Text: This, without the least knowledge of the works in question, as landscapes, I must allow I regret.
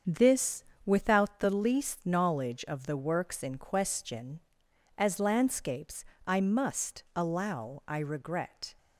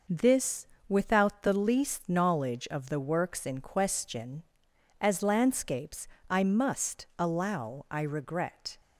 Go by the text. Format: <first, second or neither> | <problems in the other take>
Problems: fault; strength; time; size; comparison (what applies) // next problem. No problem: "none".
second | starts louder than the rest; strong; until 1.3 s; 7.5 dB